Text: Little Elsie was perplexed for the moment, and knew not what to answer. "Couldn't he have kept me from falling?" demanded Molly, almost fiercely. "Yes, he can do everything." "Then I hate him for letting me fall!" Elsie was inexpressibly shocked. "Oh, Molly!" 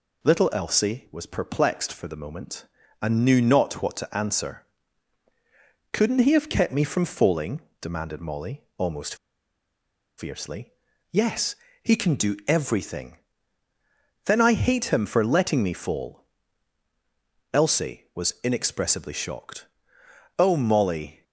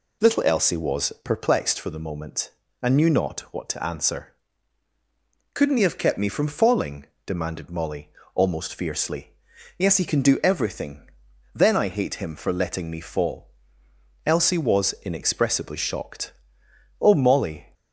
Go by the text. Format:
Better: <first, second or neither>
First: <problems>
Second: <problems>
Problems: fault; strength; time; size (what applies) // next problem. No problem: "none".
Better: second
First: pauses between "almost" and "fiercely"; at 9.1 s; 1.0 s long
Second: none